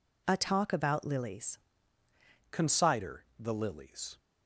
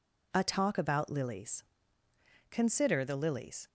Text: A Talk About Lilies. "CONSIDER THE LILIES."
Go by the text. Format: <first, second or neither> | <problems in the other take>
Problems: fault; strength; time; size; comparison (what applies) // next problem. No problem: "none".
second | changes voice at "CONSIDER"; from 2.4 s on; 1.7 s long